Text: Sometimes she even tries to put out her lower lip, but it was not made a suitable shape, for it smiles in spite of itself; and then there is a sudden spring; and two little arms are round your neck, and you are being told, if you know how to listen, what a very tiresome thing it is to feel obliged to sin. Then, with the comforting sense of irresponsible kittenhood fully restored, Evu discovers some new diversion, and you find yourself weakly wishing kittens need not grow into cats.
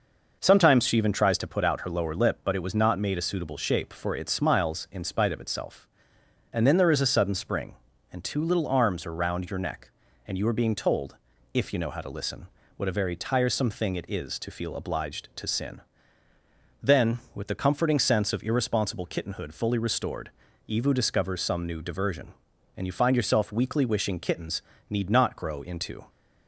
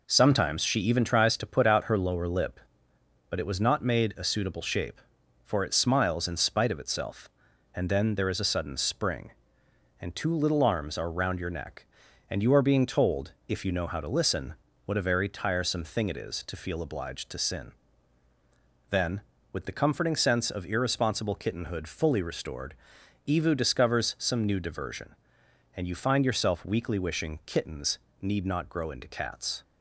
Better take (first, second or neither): second